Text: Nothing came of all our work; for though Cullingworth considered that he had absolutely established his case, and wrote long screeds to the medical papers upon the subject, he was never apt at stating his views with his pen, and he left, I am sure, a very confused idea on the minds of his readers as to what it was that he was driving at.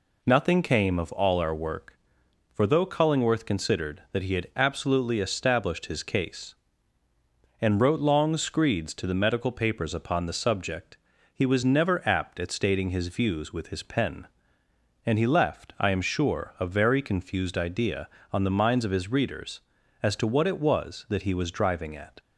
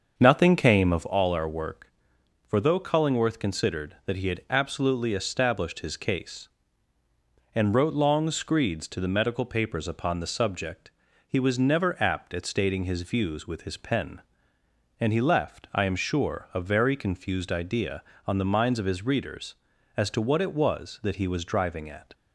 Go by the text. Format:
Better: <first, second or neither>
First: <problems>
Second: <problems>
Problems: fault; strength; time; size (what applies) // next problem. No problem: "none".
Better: first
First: none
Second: starts louder than the rest; until 1.2 s; 6.5 dB